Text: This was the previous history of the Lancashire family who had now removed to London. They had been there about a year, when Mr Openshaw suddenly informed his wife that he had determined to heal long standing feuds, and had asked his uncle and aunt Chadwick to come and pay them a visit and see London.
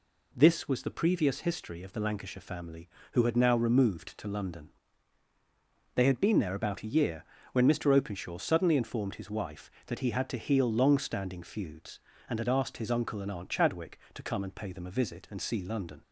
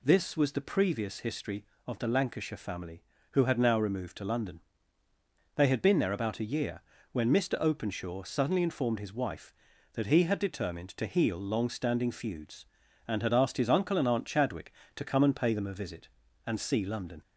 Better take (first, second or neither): second